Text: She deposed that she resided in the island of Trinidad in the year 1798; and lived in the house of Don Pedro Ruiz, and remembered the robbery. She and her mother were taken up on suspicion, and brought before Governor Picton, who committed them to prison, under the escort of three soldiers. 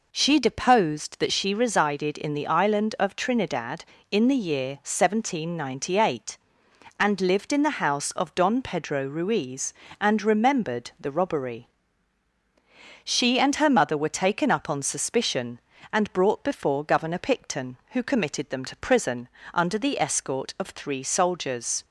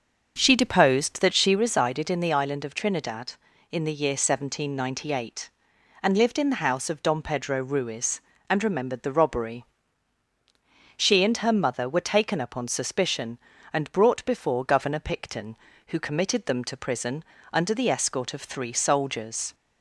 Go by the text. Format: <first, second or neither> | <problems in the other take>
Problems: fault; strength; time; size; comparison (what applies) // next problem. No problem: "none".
first | starts louder than the rest; until 1.6 s; 6.5 dB